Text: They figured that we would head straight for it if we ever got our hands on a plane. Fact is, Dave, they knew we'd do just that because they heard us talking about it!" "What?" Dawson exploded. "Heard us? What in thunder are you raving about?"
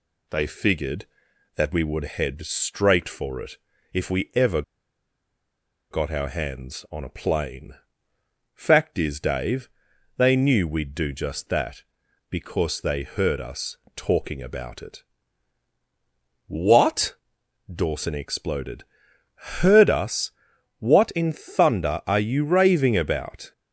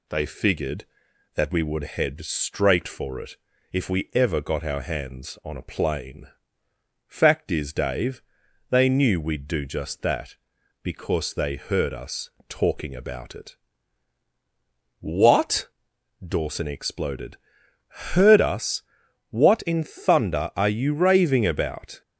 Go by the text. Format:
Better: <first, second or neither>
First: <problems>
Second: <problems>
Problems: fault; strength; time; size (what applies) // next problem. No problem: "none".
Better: second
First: pauses between "it" and "if"; slight; at 3.5 s; 0.36 s long // pauses between "ever" and "got"; strong; at 4.6 s; 1.2 s long // pauses between "us" and "talking"; slight; at 13.7 s; 0.18 s long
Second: pauses between "it" and "if"; slight; at 3.3 s; 0.36 s long // pauses between "us" and "talking"; slight; at 12.2 s; 0.18 s long